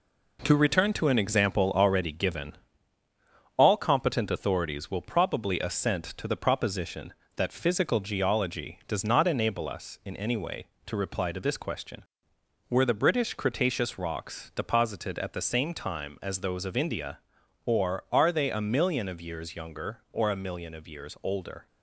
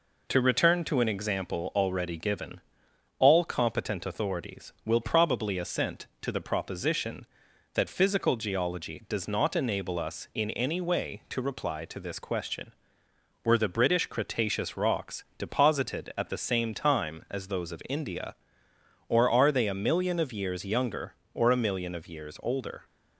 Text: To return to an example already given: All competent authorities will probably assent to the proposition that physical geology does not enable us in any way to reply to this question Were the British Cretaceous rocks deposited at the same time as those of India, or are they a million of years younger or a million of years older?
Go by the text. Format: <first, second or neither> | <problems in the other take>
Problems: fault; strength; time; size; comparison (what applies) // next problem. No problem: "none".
second | gets quieter; noticeable; throughout; 5.5 dB